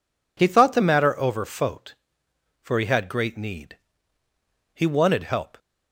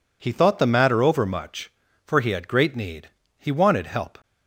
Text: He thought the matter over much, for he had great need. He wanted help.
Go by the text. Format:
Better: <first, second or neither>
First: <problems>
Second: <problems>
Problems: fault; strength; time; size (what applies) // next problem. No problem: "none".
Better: second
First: says "fote" for "much"; at 1.4 s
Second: none